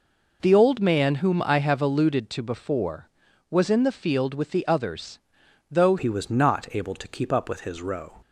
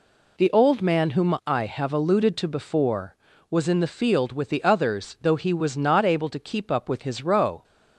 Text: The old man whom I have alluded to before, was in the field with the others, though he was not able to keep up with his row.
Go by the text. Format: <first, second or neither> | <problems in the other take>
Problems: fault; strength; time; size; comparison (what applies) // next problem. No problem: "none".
second | changes voice at "he"; from 5.9 s on; 2.3 s long